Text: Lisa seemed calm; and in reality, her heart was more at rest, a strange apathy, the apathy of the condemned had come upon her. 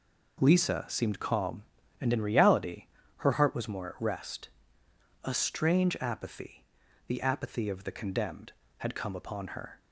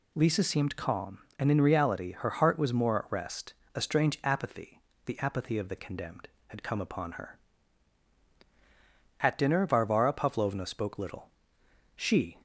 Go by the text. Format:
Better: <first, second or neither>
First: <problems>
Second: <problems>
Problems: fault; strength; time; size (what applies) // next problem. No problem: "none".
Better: first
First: none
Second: goes on to say "At dinner Varvara Pavlovna spoke little she"; strong; from 9.2 s on; 3.1 s long